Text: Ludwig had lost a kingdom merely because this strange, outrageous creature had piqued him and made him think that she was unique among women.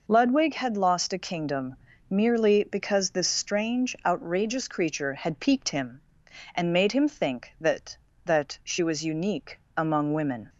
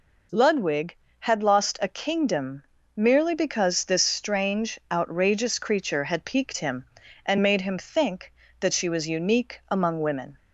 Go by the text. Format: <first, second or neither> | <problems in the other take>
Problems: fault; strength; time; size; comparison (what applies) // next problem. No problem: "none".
second | pauses between "kingdom" and "merely"; slight; at 1.7 s; 0.34 s long; slight in the second // says "that" twice; at 8.2 s // pauses between "unique" and "among"; slight; at 9.5 s; 0.18 s long